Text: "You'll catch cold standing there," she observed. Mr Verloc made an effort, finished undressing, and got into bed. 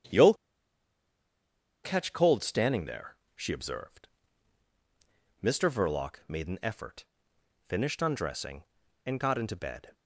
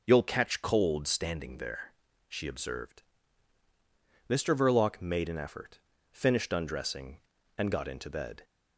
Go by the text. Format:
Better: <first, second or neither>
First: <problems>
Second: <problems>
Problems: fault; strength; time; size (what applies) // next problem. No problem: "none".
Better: second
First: starts louder than the rest; strong; until 2.6 s; 9 dB // pauses between "You'll" and "catch"; strong; at 0.3 s; 1.5 s long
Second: none